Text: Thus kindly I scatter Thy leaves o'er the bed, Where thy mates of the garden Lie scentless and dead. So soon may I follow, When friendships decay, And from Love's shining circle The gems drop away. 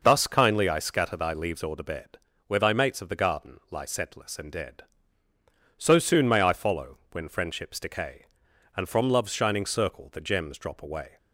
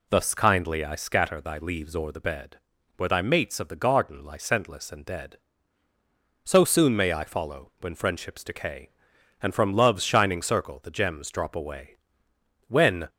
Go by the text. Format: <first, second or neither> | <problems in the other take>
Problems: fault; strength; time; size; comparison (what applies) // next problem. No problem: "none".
first | goes on to say "When"; slight; from 12.6 s on; 0.40 s long